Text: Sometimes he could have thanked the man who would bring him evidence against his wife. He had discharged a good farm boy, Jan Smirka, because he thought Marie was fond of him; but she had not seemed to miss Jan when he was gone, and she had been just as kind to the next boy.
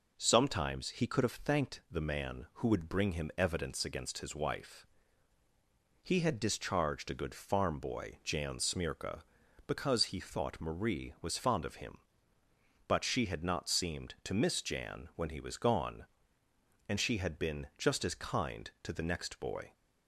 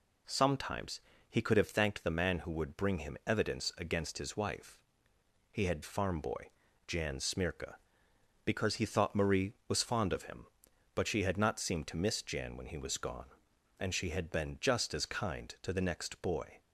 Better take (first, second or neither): first